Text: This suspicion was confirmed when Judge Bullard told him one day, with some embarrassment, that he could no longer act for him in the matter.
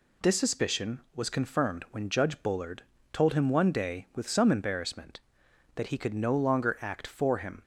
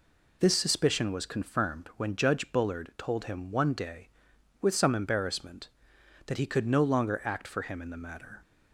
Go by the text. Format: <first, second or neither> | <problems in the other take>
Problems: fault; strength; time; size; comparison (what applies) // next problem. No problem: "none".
second | pauses between "Bullard" and "told"; slight; at 2.8 s; 0.30 s long // stops before "in the matter"; at 7.6 s